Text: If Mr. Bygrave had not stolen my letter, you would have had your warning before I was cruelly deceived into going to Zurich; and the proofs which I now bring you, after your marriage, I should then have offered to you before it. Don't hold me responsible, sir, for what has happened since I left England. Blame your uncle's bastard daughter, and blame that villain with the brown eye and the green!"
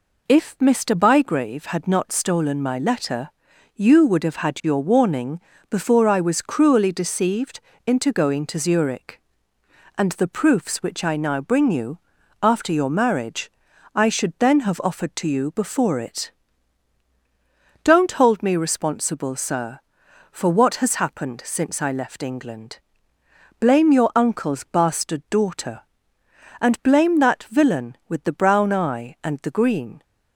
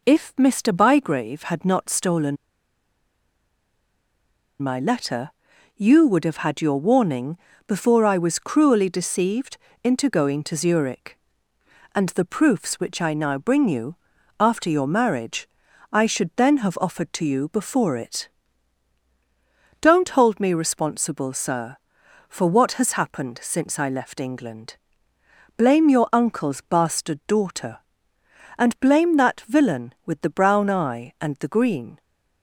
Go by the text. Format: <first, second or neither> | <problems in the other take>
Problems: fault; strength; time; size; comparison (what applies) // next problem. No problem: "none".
first | pauses between "stolen" and "my"; strong; at 2.3 s; 2.2 s long // pauses between "warning" and "before"; slight; at 7.3 s; 0.32 s long; slight in the first // pauses between "deceived" and "into"; slight; at 9.5 s; 0.28 s long; slight in the first